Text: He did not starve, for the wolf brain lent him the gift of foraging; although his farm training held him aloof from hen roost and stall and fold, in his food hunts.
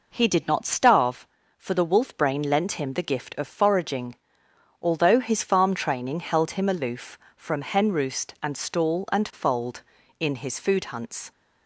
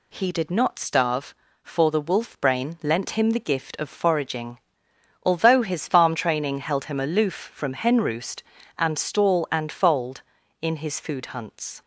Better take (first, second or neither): neither